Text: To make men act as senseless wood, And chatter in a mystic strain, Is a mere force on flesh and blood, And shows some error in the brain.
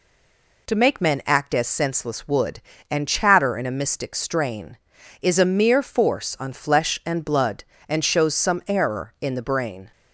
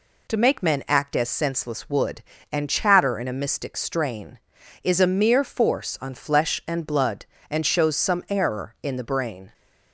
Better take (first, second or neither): second